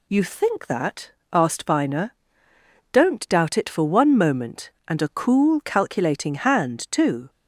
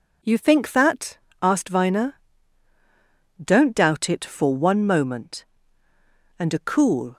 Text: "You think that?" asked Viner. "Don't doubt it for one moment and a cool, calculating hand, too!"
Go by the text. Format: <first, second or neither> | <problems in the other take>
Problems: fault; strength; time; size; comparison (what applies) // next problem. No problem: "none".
first | stops before "calculating hand too"; at 7.1 s